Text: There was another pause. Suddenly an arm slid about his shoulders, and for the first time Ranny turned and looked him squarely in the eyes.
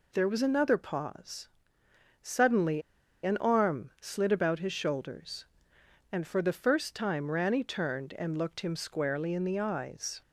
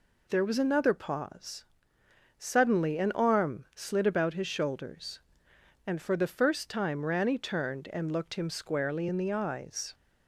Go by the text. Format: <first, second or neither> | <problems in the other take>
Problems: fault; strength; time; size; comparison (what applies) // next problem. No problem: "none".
second | pauses between "Suddenly" and "an"; at 2.8 s; 0.42 s long